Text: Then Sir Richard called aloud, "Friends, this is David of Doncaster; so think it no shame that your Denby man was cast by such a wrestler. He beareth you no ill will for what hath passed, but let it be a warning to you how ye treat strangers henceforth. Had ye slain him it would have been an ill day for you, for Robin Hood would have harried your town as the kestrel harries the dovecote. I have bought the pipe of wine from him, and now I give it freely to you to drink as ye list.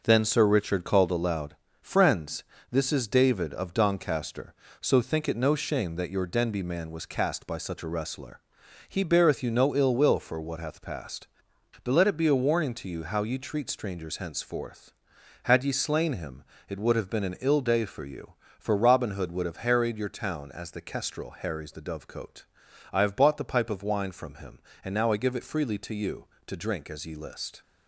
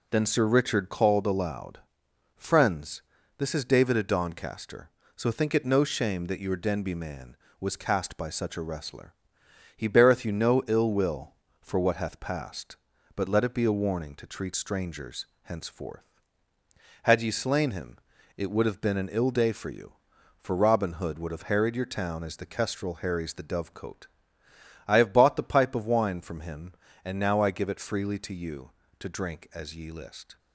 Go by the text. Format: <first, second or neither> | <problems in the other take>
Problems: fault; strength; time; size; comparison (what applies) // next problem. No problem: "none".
first | skips "you how ye"; at 14.2 s // pauses between "strangers" and "henceforth"; slight; at 15.2 s; 0.16 s long // pauses between "him" and "it"; at 17.9 s; 0.40 s long; slight in the first